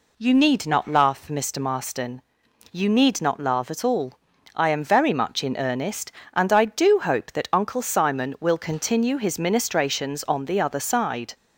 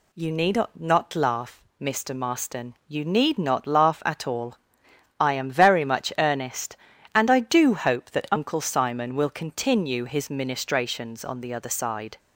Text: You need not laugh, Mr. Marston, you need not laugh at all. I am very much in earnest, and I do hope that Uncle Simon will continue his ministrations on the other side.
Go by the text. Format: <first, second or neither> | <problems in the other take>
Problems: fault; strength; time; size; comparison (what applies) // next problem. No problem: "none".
first | pauses between "need" and "not"; slight; at 0.6 s; 0.16 s long // skips "in"; at 6.1 s